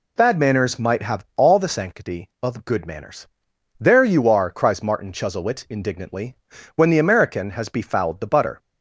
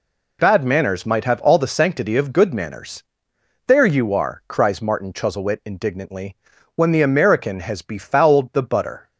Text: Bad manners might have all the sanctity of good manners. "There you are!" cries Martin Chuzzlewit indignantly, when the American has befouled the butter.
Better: neither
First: none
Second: none

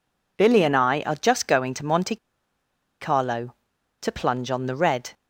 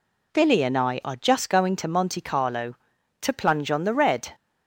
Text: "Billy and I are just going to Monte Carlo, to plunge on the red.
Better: second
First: pauses between "Monte" and "Carlo"; noticeable; at 2.1 s; 0.84 s long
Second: none

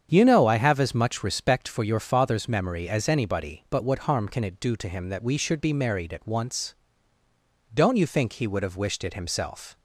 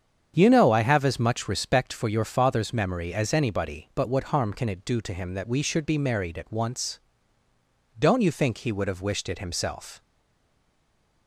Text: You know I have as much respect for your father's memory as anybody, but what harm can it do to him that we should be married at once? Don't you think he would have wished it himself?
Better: first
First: starts louder than the rest; strong; until 1.1 s; 8 dB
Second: starts louder than the rest; strong; until 1.3 s; 8 dB // stays silent after the last word; noticeable; from 10.0 s on; 1.2 s long

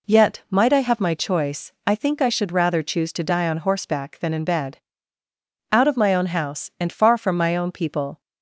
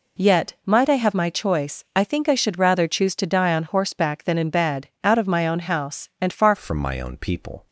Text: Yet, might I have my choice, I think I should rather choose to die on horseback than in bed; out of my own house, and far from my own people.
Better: first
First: none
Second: changes voice at "from"; from 6.5 s on; 1.1 s long

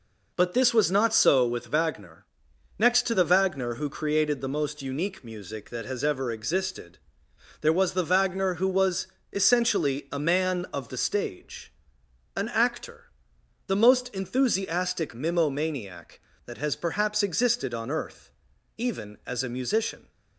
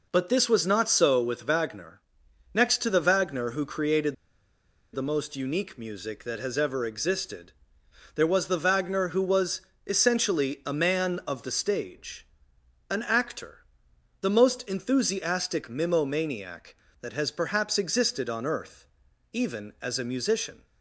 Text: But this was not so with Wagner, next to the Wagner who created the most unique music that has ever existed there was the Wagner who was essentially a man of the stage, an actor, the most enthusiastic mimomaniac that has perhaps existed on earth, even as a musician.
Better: first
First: pauses between "existed" and "there"; noticeable; at 6.9 s; 0.62 s long // pauses between "was" and "essentially"; slight; at 9.0 s; 0.26 s long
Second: pauses between "created" and "the"; noticeable; at 4.1 s; 0.78 s long // pauses between "existed" and "there"; noticeable; at 7.5 s; 0.62 s long // pauses between "was" and "essentially"; slight; at 9.5 s; 0.26 s long

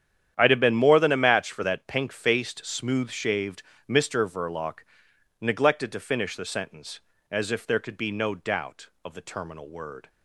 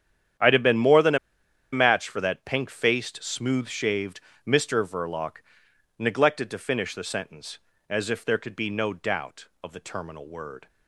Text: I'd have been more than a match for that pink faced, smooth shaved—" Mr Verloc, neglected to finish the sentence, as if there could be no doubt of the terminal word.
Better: first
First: starts louder than the rest; strong; until 1.3 s; 9.5 dB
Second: starts louder than the rest; strong; until 1.9 s; 9.5 dB // pauses between "a" and "match"; noticeable; at 1.1 s; 0.55 s long

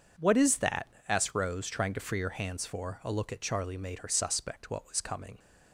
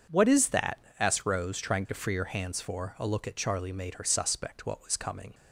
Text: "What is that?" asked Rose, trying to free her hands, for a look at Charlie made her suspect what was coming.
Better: neither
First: none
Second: none

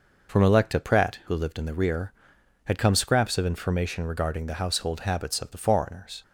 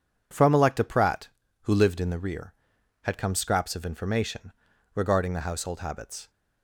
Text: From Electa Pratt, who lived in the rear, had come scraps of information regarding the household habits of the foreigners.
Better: first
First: none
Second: starts louder than the rest; strong; until 1.6 s; 8.5 dB // stops before "of the foreigners"; at 6.2 s

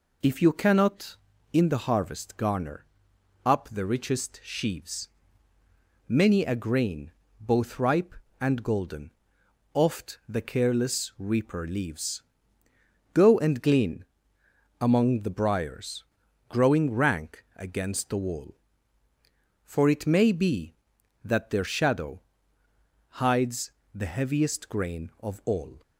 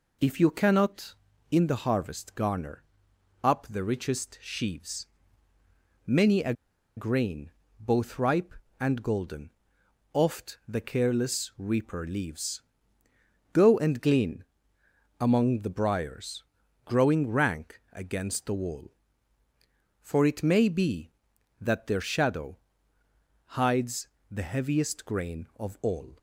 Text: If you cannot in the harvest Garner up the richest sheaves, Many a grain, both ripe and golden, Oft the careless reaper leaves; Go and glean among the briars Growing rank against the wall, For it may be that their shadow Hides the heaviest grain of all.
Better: first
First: pauses between "Garner" and "up"; noticeable; at 2.8 s; 0.60 s long // pauses between "glean" and "among"; noticeable; at 14.0 s; 0.74 s long // pauses between "briars" and "Growing"; at 16.0 s; 0.42 s long // pauses between "shadow" and "Hides"; noticeable; at 22.2 s; 0.98 s long // pauses between "Hides" and "the"; slight; at 23.7 s; 0.22 s long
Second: pauses between "Garner" and "up"; noticeable; at 2.8 s; 0.60 s long // pauses between "a" and "grain"; at 6.5 s; 0.44 s long // pauses between "glean" and "among"; noticeable; at 14.4 s; 0.74 s long // pauses between "briars" and "Growing"; at 16.4 s; 0.40 s long // pauses between "shadow" and "Hides"; noticeable; at 22.5 s; 0.98 s long // pauses between "Hides" and "the"; slight; at 24.0 s; 0.22 s long

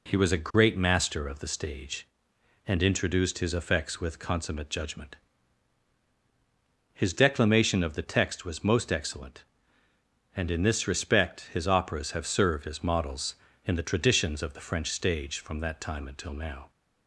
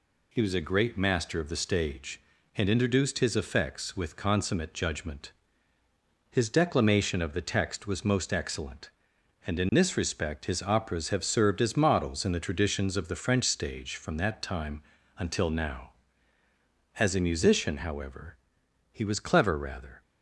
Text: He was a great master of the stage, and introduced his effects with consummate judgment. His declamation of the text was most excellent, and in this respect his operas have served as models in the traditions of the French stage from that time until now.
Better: first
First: none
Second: pauses between "time" and "until"; slight; at 14.8 s; 0.34 s long // goes on to say "As a musician however he was clever rather"; strong; from 16.9 s on; 3.0 s long

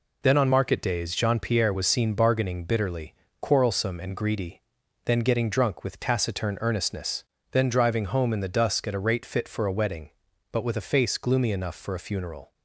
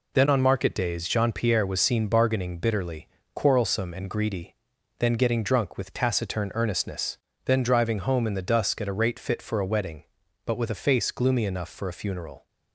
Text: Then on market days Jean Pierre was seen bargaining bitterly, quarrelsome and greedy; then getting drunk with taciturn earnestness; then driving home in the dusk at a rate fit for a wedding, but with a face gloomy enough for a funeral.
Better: neither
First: none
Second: none

